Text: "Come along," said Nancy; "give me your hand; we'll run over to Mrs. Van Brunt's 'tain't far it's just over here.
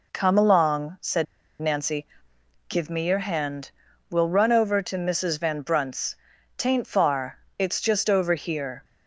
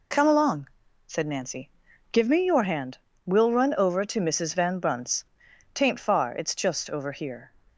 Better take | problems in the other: second | pauses between "said" and "Nancy"; at 1.2 s; 0.36 s long // pauses between "Brunt's" and "tain't"; at 6.1 s; 0.42 s long; noticeable in the second // pauses between "far" and "it's"; slight; at 7.3 s; 0.20 s long

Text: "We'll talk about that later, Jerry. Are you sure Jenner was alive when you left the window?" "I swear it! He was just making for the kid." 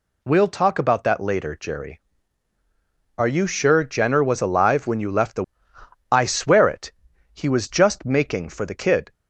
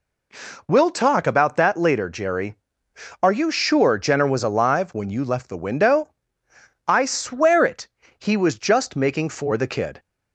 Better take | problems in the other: second | skips "window"; at 5.7 s

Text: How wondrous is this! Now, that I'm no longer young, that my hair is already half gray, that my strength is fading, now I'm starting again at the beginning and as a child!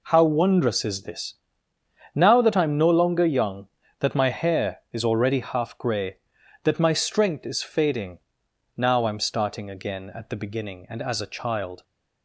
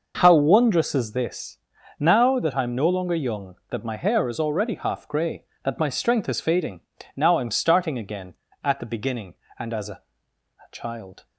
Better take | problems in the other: first | says "a" twice; at 9.9 s

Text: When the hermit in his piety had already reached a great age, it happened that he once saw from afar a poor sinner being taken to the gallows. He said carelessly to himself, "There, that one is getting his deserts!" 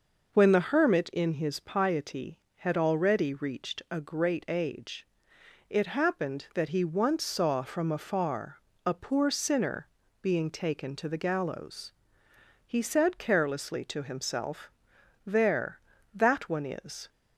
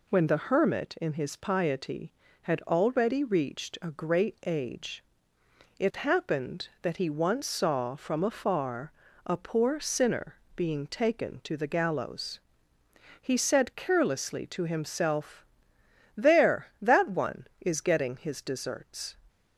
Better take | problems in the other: second | pauses between "afar" and "a"; slight; at 8.6 s; 0.26 s long; slight in the second // pauses between "sinner" and "being"; slight; at 9.8 s; 0.34 s long; slight in the second // stops before "getting his deserts"; at 17.0 s

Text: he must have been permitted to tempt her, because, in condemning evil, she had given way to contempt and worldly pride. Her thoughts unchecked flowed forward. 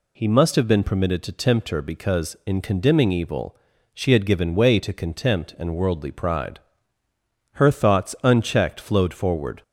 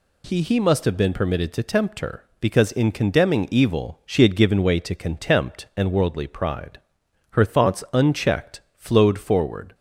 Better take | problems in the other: first | says "he" twice; at 0.4 s // pauses between "unchecked" and "flowed"; slight; at 8.6 s; 0.16 s long

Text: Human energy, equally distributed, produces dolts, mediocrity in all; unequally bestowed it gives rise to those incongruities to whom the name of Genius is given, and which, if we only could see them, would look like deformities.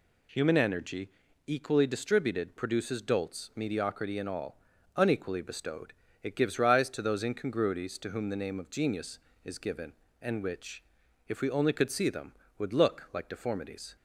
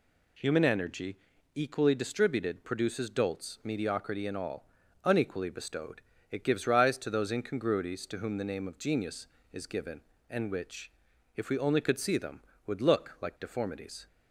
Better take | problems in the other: neither | pauses between "bestowed" and "it"; slight; the same in both

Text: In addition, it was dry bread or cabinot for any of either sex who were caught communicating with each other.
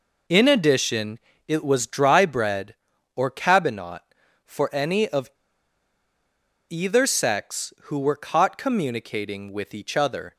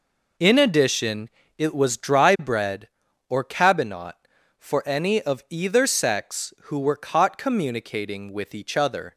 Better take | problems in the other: second | pauses between "of" and "either"; strong; at 5.2 s; 1.4 s long

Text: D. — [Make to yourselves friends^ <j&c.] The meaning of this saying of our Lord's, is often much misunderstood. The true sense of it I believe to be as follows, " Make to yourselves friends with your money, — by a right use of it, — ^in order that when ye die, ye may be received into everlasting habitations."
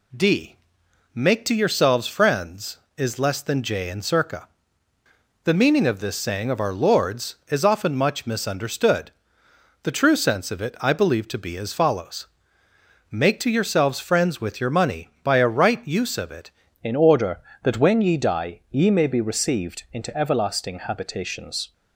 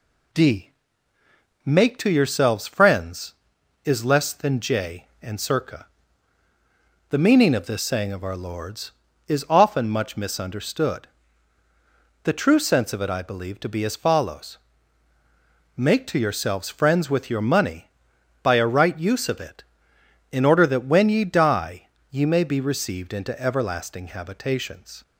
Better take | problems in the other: second | changes voice at "in"; from 16.8 s on; 4.9 s long

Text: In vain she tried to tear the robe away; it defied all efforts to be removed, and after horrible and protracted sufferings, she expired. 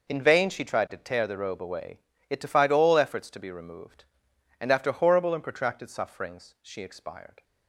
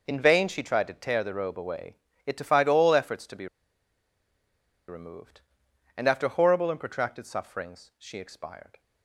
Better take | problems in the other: first | pauses between "be" and "removed"; strong; at 3.4 s; 1.4 s long

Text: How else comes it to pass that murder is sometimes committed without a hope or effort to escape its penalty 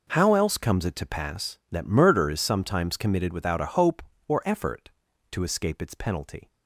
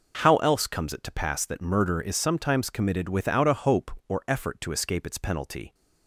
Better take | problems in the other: neither | none

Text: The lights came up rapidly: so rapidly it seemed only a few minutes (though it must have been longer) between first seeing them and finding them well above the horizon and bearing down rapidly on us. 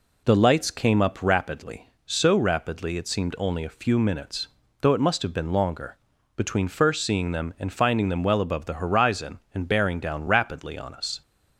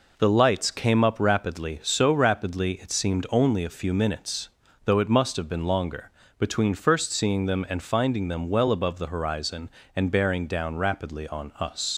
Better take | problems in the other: first | leaves "us" unfinished; at 11.9 s; 90 ms

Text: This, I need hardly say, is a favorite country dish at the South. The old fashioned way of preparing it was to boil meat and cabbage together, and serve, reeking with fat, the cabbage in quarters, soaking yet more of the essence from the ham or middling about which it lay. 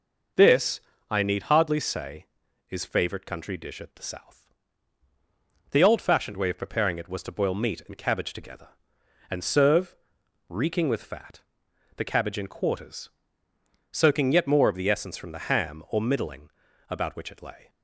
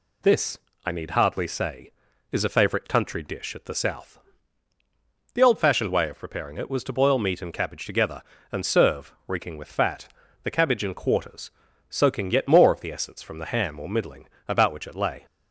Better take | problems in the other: second | skips "a"; at 2.8 s // pauses between "middling" and "about"; at 16.4 s; 0.40 s long; slight in the second

